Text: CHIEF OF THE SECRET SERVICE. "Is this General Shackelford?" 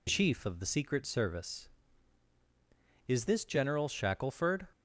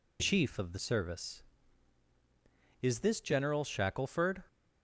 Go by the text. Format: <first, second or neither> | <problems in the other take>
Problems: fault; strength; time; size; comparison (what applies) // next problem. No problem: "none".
first | skips "SECRET"; at 0.7 s